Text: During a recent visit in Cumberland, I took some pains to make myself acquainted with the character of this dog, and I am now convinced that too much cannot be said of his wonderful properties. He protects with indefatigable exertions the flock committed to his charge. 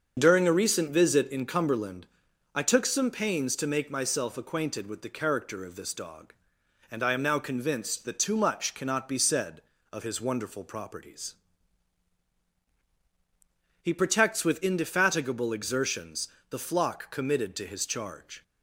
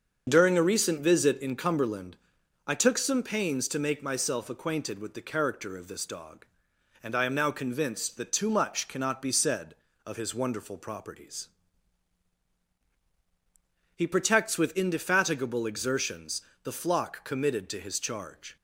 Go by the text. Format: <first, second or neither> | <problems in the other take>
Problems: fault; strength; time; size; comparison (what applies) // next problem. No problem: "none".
neither | starts louder than the rest; the same in both // pauses between "exertions" and "the"; slight; the same in both